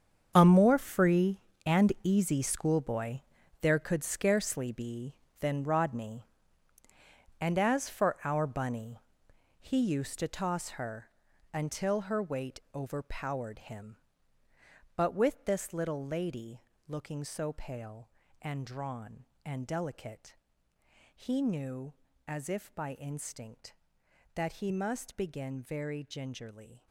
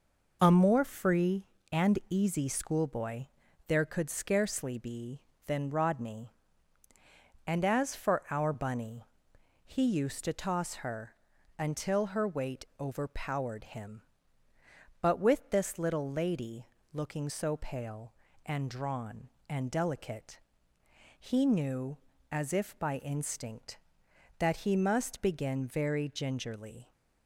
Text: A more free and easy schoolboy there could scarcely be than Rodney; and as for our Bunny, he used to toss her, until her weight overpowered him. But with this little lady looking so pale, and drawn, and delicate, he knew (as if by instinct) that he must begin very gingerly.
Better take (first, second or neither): second